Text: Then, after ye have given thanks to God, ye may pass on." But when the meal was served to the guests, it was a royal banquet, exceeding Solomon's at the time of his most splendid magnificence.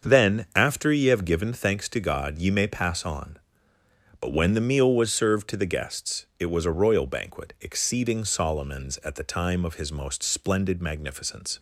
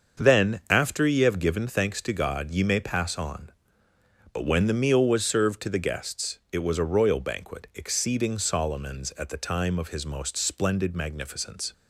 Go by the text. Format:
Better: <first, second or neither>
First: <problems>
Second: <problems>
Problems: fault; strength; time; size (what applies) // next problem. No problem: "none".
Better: neither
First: starts louder than the rest; until 1.1 s; 6.5 dB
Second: starts louder than the rest; until 1.2 s; 6.5 dB